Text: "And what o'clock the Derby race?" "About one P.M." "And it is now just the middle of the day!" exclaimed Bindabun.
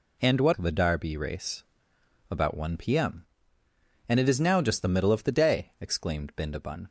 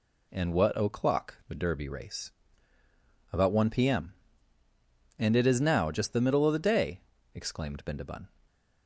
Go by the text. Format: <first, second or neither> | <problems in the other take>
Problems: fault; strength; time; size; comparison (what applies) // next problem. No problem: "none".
second | skips "o'clock"; at 0.5 s